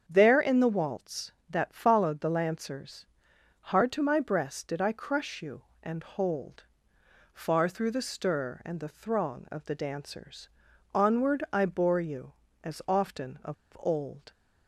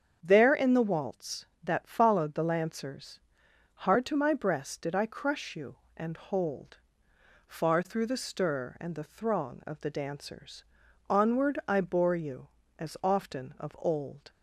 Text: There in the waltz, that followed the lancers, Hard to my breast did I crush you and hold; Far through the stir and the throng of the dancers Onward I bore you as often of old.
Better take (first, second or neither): second